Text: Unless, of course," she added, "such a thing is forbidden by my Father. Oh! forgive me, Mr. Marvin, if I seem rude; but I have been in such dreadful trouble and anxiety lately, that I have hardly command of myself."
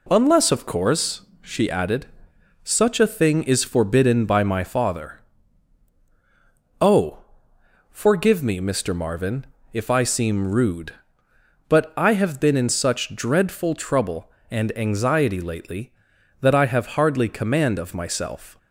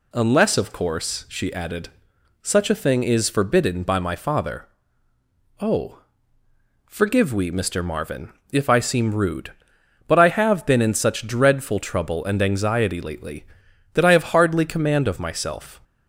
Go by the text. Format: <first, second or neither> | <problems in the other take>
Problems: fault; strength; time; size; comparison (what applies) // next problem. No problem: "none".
first | says "we" for "me"; at 7.3 s